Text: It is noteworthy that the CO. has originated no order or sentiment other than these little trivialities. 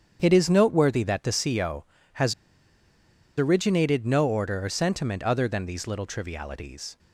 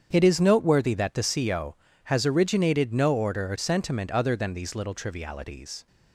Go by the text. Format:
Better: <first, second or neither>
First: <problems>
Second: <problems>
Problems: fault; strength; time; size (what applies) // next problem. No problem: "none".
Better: second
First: starts louder than the rest; strong; until 1.2 s; 8 dB // pauses between "has" and "originated"; at 2.3 s; 1.0 s long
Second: starts louder than the rest; strong; until 1.1 s; 8 dB